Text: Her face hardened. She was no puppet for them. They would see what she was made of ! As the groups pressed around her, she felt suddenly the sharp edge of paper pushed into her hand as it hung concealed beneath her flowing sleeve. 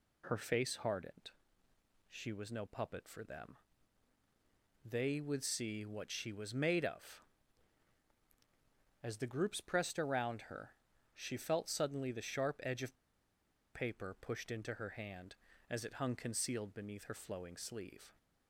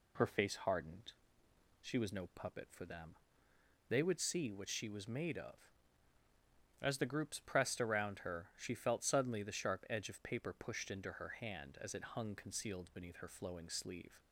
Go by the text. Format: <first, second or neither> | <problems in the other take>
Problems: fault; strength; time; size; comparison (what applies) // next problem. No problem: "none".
second | pauses between "of" and "paper"; noticeable; at 12.9 s; 0.77 s long